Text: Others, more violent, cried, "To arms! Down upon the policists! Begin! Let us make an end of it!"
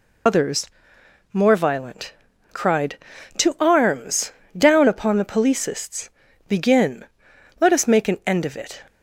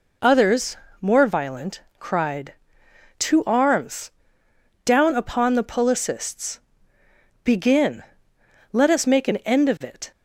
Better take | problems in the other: second | loses the start of "Others"; at 0.2 s; 70 ms

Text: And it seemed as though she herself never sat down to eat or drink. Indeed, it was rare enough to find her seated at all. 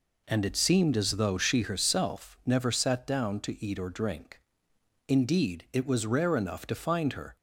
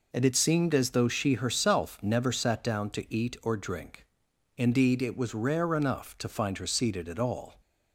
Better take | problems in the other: second | stops before "seated at all"; at 7.3 s

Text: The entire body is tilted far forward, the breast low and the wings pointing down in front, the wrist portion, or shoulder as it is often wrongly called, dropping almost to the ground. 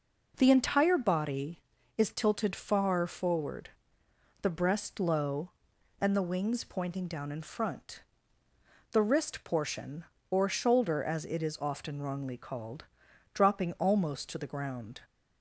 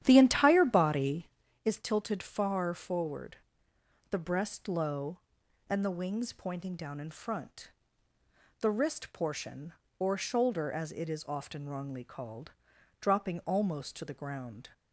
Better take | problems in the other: first | starts louder than the rest; strong; until 1.6 s; 11 dB

